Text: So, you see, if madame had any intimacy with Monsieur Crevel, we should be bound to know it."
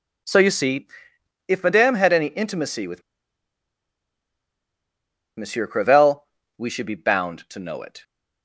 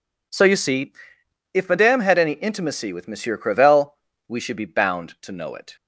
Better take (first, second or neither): second